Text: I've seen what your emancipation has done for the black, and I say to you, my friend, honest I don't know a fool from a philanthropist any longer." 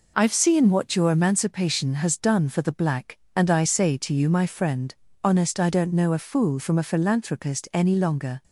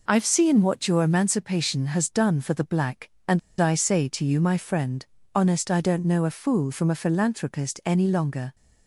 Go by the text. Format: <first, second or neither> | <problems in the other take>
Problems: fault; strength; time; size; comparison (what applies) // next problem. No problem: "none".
first | pauses between "and" and "I"; slight; at 3.3 s; 0.21 s long